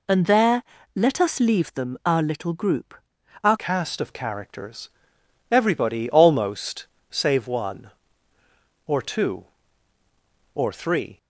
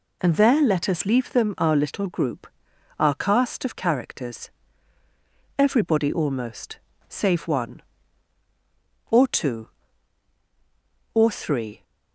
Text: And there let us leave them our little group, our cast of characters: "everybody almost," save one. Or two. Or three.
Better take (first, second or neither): second